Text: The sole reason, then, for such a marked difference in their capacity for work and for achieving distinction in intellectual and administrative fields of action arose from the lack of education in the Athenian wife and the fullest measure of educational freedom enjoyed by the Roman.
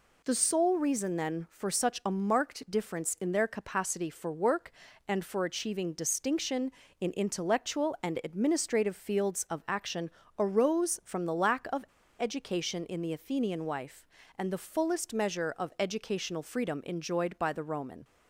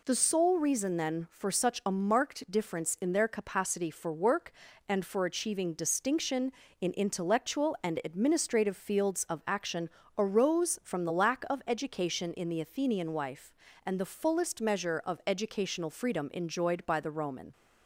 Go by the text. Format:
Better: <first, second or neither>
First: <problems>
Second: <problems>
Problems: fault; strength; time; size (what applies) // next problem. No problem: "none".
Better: second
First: pauses between "action" and "arose"; slight; at 10.1 s; 0.28 s long // pauses between "of" and "education"; slight; at 11.8 s; 0.35 s long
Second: pauses between "action" and "arose"; slight; at 9.8 s; 0.28 s long